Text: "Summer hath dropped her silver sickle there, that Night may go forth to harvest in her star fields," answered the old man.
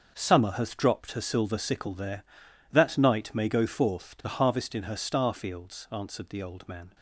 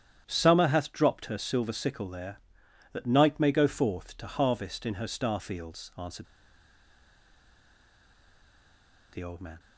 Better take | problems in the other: first | starts louder than the rest; strong; until 1.2 s; 9.5 dB; also in the first // pauses between "answered" and "the"; strong; at 6.2 s; 2.8 s long

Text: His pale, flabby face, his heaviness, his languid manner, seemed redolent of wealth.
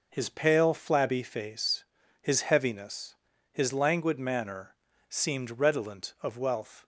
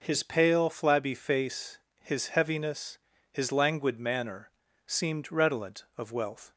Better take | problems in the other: neither | none

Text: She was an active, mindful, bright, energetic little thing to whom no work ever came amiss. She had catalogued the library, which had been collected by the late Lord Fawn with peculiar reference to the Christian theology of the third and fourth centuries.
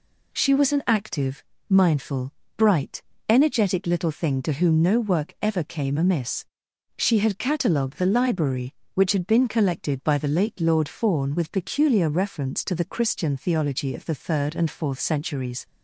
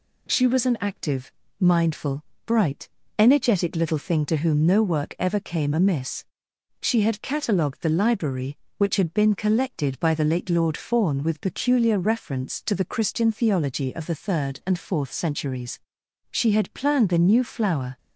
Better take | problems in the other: first | goes on to say "She had planned the new flower"; strong; from 16.2 s on; 1.6 s long

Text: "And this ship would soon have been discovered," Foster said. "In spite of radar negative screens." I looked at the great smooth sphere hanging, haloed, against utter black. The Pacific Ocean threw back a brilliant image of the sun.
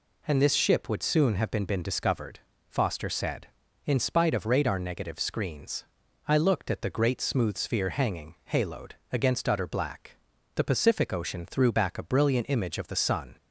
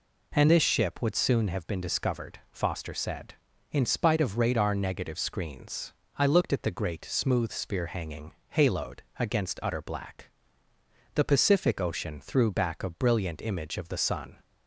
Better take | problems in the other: second | says "been" twice; at 1.6 s

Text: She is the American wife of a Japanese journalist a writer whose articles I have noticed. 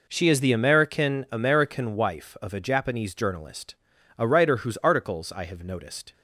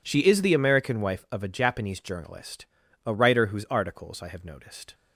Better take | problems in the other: second | says "American" twice; at 1.3 s // pauses between "journalist" and "a"; noticeable; at 3.7 s; 0.46 s long; also in the second

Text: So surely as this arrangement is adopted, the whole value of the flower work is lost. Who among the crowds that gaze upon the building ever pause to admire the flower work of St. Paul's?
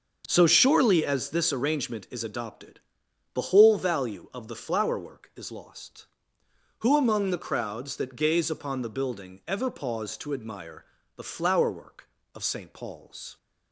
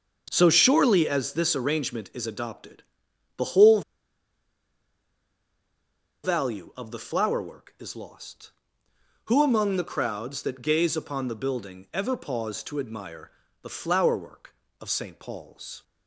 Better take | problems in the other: first | starts louder than the rest; until 1.3 s; 6.5 dB; also in the first // pauses between "whole" and "value"; strong; at 3.8 s; 2.4 s long // pauses between "admire" and "the"; slight; at 13.3 s; 0.32 s long; slight in the first

